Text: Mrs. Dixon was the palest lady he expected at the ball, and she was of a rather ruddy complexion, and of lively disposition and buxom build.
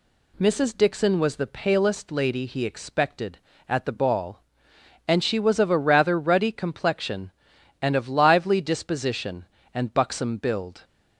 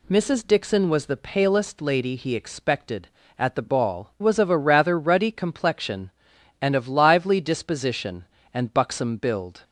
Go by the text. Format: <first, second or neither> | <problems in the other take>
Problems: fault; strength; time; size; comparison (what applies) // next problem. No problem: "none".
first | skips "and she"; at 4.1 s